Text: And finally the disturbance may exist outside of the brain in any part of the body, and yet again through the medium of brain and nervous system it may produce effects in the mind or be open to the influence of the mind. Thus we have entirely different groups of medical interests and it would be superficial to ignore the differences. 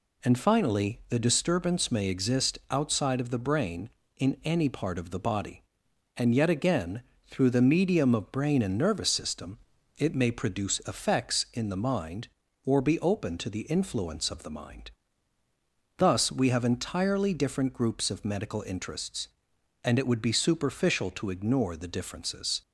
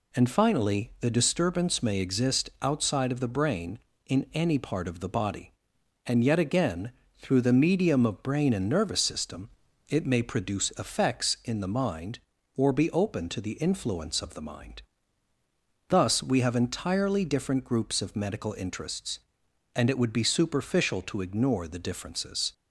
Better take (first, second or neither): neither